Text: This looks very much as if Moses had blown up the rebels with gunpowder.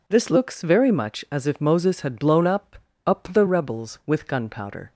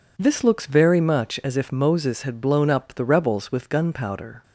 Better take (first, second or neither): second